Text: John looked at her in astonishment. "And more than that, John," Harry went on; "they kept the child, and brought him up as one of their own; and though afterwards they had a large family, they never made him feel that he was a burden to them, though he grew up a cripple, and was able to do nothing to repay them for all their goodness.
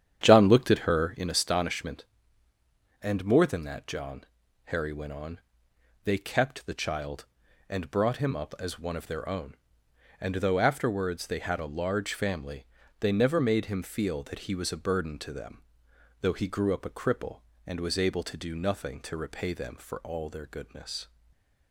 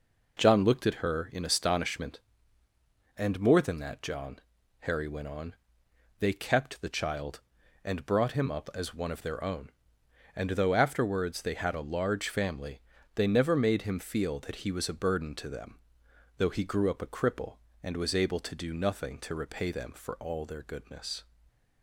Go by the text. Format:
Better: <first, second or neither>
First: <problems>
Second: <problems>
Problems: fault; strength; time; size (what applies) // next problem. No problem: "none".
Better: second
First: starts louder than the rest; strong; until 1.4 s; 9.5 dB // stays silent after the last word; slight; from 21.0 s on; 0.7 s long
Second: stays silent after the last word; slight; from 21.2 s on; 0.6 s long